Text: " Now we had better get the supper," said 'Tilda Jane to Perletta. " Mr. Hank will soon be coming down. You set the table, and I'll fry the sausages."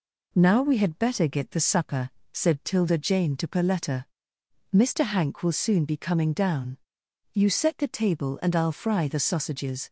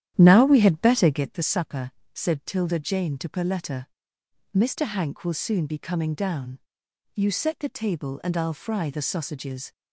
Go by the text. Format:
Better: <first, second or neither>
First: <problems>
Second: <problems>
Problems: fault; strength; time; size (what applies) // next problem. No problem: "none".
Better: first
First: none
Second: starts louder than the rest; strong; until 1.4 s; 11 dB